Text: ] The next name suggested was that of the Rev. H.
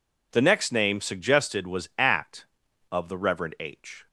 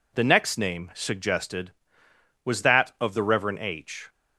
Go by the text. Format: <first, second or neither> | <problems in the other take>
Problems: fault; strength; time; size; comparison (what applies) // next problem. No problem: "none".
second | says "at" for "that"; at 1.9 s